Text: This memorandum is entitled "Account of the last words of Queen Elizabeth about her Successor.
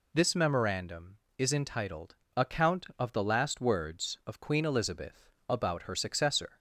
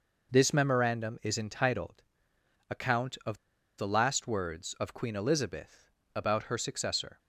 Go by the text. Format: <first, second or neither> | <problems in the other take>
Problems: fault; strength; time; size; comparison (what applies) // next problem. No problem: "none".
first | pauses between "entitled" and "Account"; noticeable; at 2.0 s; 0.66 s long; slight in the first // pauses between "of" and "the"; at 3.3 s; 0.40 s long // pauses between "Elizabeth" and "about"; slight; at 5.9 s; 0.24 s long; slight in the first